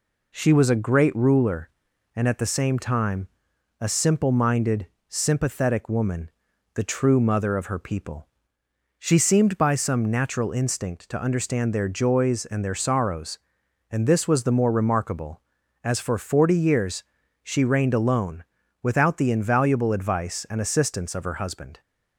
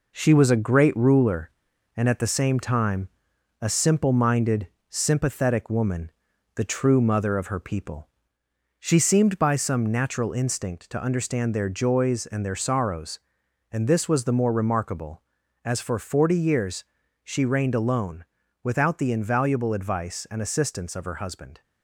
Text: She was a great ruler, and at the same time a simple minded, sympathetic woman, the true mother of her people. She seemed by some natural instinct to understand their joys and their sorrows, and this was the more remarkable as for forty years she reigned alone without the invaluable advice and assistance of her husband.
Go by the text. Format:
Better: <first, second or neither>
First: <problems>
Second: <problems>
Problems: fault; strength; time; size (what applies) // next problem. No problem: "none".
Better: first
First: pauses between "time" and "a"; noticeable; at 3.2 s; 0.50 s long // pauses between "years" and "she"; at 17.0 s; 0.40 s long // pauses between "alone" and "without"; at 18.4 s; 0.38 s long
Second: gets quieter; noticeable; throughout; 5 dB // pauses between "time" and "a"; noticeable; at 3.0 s; 0.50 s long // pauses between "years" and "she"; at 16.8 s; 0.40 s long // pauses between "alone" and "without"; at 18.2 s; 0.38 s long